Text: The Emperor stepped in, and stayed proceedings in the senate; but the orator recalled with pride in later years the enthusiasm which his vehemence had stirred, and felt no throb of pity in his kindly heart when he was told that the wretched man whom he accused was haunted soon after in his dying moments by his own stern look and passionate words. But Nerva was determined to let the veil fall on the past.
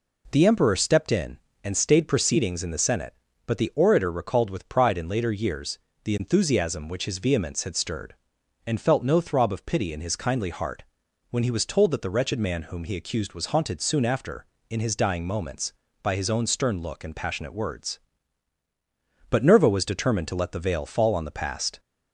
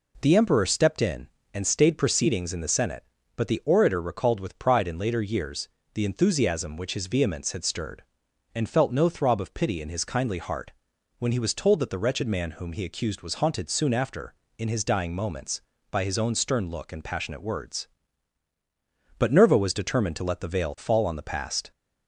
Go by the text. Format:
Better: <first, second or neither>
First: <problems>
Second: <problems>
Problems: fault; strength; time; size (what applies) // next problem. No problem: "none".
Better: neither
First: pauses between "years" and "the"; slight; at 5.7 s; 0.24 s long // pauses between "heart" and "when"; noticeable; at 10.8 s; 0.46 s long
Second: pauses between "years" and "the"; slight; at 5.6 s; 0.24 s long // pauses between "heart" and "when"; noticeable; at 10.7 s; 0.46 s long